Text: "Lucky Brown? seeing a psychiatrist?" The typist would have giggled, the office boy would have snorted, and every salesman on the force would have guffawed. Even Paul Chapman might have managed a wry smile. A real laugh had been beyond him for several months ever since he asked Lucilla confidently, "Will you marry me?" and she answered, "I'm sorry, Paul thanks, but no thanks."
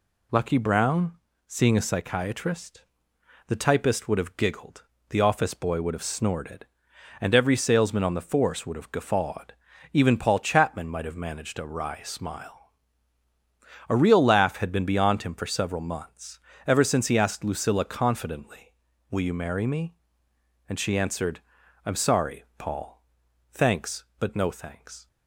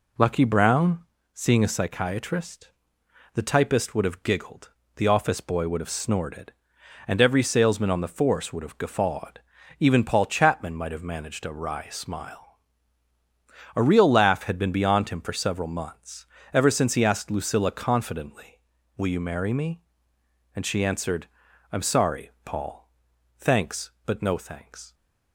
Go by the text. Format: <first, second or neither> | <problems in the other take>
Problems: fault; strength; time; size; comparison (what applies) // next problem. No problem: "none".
first | starts louder than the rest; slight; until 1.2 s; 3.5 dB // pauses between "months" and "ever"; slight; at 16.2 s; 0.28 s long; slight in the first // pauses between "Paul" and "thanks"; noticeable; at 22.8 s; 0.48 s long; noticeable in the first